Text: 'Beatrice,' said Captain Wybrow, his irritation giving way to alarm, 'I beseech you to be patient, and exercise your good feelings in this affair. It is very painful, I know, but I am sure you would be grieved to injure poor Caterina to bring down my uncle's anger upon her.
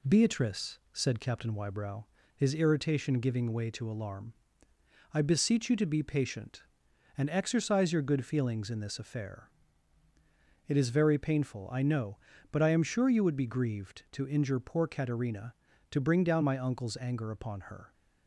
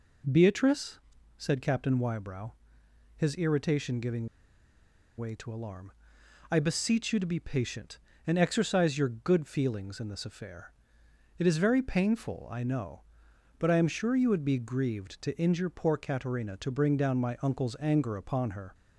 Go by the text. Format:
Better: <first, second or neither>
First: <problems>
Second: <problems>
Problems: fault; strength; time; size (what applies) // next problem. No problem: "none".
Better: first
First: none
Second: pauses between "giving" and "way"; noticeable; at 4.2 s; 0.91 s long